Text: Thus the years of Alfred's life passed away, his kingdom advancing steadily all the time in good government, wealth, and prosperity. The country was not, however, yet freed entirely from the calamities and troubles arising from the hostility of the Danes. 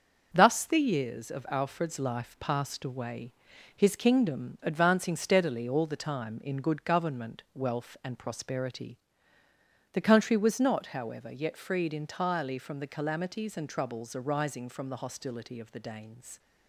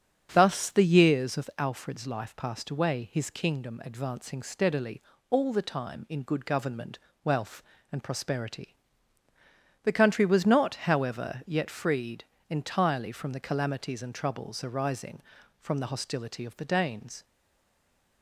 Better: first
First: starts louder than the rest; until 1.3 s; 6.5 dB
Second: starts louder than the rest; strong; until 1.3 s; 8 dB // pauses between "steadily" and "all"; slight; at 5.0 s; 0.26 s long // pauses between "freed" and "entirely"; slight; at 12.2 s; 0.26 s long // stays silent after the last word; from 17.2 s on; 1.0 s long

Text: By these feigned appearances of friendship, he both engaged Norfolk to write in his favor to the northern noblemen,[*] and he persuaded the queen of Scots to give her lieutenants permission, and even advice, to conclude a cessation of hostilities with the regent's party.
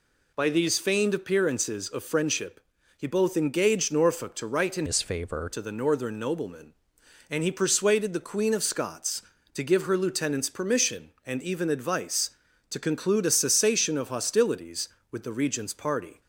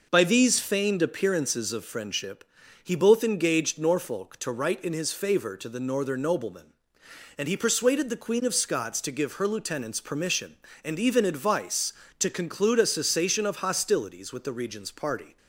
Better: second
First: changes voice from "his" to "favor"; from 4.8 to 5.4 s; 0.6 s long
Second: none

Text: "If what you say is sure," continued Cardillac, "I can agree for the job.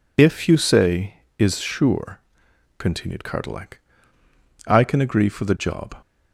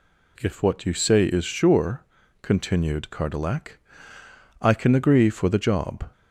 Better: second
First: skips "what"; at 0.4 s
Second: none

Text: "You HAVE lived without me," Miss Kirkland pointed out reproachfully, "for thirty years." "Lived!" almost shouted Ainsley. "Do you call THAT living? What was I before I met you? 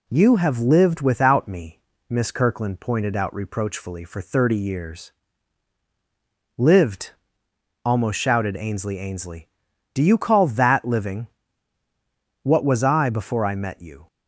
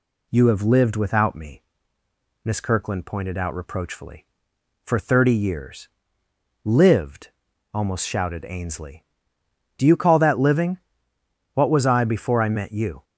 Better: second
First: says "Ainsley" twice; at 8.9 s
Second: none

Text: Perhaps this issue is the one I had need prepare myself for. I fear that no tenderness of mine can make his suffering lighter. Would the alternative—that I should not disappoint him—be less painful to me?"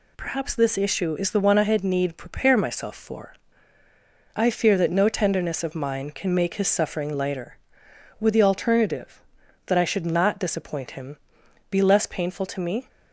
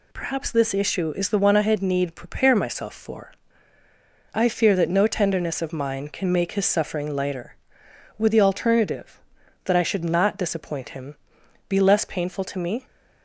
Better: neither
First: none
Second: none

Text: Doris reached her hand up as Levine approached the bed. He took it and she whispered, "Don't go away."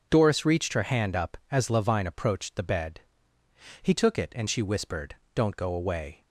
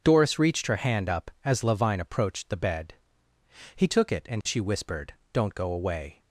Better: neither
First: none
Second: none

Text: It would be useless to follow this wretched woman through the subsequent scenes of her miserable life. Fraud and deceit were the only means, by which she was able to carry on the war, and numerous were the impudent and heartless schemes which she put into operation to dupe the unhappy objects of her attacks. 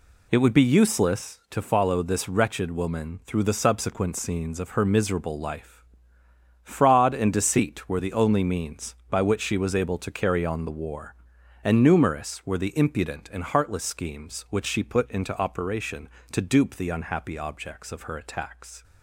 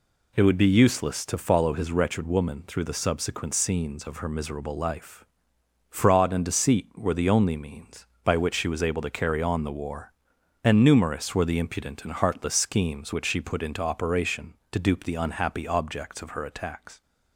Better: first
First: none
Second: says "his" for "this"; at 1.7 s

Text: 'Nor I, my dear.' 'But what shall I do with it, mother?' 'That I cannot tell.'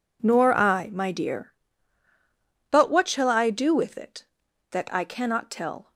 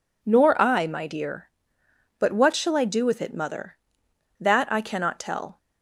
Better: second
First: skips "mother"; at 4.4 s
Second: none

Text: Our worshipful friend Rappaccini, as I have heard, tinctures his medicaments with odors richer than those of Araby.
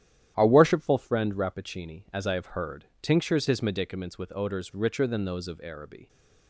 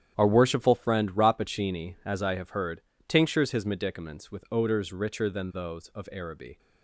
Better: neither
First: starts louder than the rest; strong; until 1.3 s; 11 dB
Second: starts louder than the rest; strong; until 1.1 s; 9.5 dB

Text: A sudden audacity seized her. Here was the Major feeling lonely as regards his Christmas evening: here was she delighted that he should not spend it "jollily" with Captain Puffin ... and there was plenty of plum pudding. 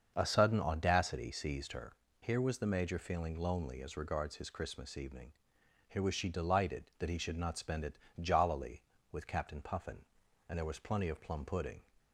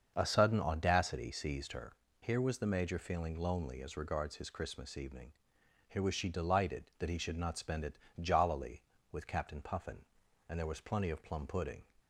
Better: neither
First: starts louder than the rest; until 1.1 s; 6.5 dB // pauses between "it" and "jollily"; slight; at 7.9 s; 0.22 s long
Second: starts louder than the rest; until 1.1 s; 6.5 dB // pauses between "it" and "jollily"; slight; at 7.9 s; 0.22 s long

